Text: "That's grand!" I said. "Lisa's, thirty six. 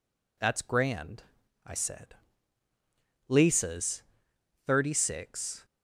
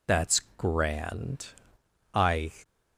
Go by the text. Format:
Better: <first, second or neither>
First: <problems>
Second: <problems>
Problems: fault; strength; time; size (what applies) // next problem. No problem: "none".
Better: first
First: none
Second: pauses between "That's" and "grand"; slight; at 0.4 s; 0.16 s long // stops before "said Lisa's thirty six"; at 2.6 s